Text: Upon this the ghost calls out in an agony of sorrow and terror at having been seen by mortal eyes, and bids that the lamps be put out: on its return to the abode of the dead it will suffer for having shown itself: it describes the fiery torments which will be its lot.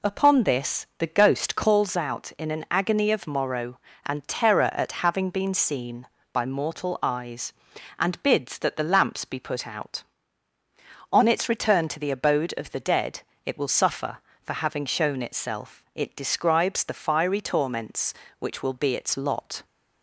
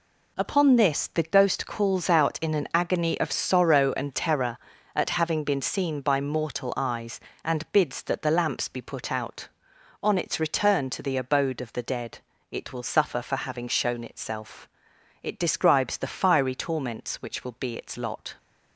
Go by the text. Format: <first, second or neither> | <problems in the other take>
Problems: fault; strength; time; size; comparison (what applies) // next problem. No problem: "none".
second | says "morrow" for "sorrow"; at 3.2 s // pauses between "dead" and "it"; slight; at 13.2 s; 0.24 s long; slight in the second